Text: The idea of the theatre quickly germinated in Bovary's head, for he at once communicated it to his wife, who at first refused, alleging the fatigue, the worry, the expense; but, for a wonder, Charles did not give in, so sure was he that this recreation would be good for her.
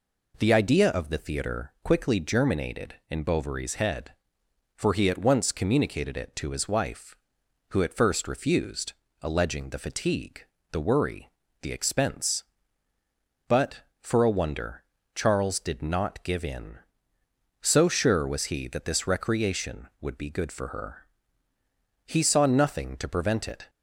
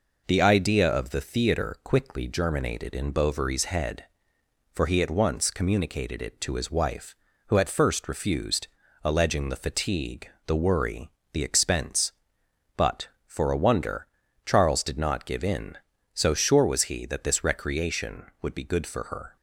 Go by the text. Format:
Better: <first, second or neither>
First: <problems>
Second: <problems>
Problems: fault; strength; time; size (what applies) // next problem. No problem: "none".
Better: second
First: goes on to say "He saw nothing to prevent it"; from 22.0 s on; 1.6 s long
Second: none